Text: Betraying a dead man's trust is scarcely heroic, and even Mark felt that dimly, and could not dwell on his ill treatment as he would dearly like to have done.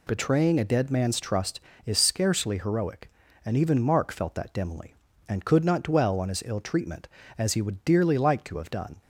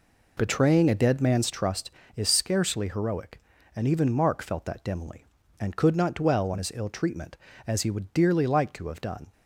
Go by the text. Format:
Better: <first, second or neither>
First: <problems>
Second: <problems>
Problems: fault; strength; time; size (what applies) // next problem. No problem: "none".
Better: first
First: none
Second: starts louder than the rest; until 1.5 s; 4 dB